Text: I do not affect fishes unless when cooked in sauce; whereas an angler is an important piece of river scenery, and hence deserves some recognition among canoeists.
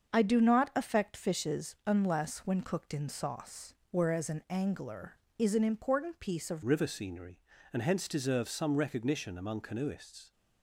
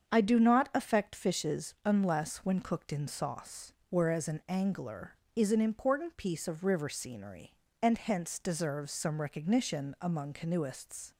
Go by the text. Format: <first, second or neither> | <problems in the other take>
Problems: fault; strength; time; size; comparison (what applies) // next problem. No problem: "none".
second | starts louder than the rest; until 1.1 s; 6.5 dB; strong in the second // changes voice at "river"; from 6.6 s on; 3.7 s long